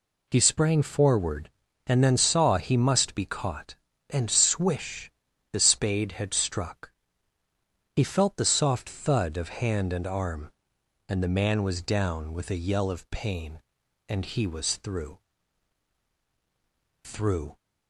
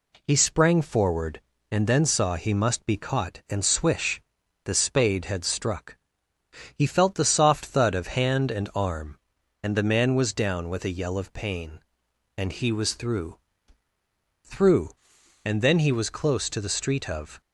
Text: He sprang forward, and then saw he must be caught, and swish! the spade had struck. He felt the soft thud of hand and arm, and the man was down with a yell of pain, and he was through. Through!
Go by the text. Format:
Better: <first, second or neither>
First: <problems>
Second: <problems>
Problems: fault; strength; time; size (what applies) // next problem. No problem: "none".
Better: first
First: none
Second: goes on to say "And then he was close to the street of"; strong; from 15.4 s on; 1.9 s long